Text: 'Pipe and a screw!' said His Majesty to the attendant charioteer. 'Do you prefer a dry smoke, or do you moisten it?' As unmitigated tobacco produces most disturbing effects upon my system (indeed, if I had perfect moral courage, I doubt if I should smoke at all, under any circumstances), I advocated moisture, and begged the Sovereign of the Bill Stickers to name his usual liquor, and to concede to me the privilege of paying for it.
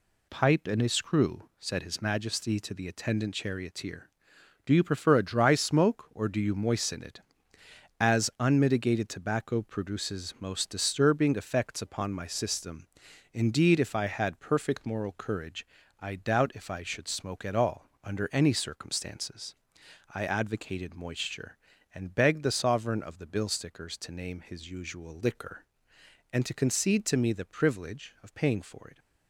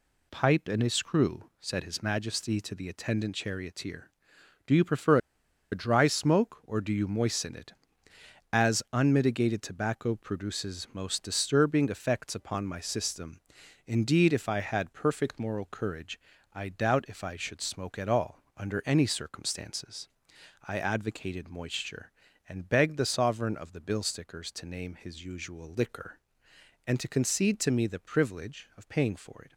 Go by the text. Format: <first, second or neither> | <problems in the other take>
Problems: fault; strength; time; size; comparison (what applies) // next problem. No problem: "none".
first | pauses between "prefer" and "a"; noticeable; at 5.1 s; 0.54 s long